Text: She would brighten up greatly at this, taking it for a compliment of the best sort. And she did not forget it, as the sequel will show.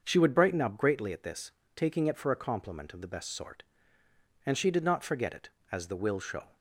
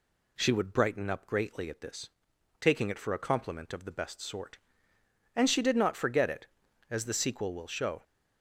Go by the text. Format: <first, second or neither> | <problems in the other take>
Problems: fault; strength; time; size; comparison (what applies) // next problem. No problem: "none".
second | starts louder than the rest; until 1.0 s; 6.5 dB // skips "sequel"; at 5.9 s